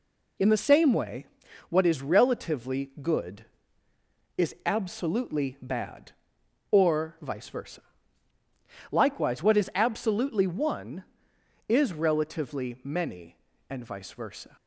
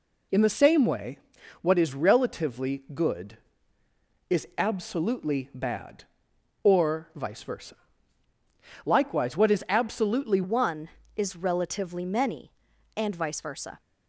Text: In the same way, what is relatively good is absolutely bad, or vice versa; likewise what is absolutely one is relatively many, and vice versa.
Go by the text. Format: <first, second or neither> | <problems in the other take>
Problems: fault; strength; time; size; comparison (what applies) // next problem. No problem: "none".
first | changes voice at "one"; from 10.4 s on; 3.4 s long